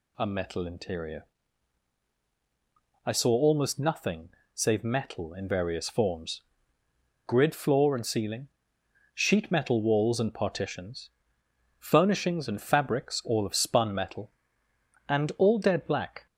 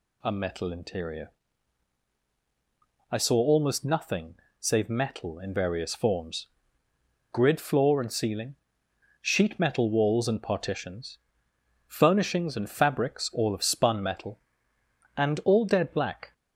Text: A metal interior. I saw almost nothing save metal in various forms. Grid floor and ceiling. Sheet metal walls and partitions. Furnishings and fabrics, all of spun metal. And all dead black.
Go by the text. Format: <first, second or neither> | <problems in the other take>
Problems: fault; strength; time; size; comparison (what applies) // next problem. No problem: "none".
neither | pauses between "nothing" and "save"; slight; the same in both